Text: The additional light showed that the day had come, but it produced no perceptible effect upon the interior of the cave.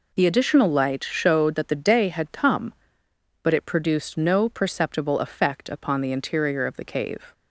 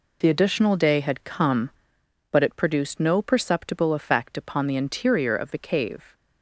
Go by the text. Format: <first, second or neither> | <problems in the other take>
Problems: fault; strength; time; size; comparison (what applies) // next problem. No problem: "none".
first | skips "light showed that the"; at 0.7 s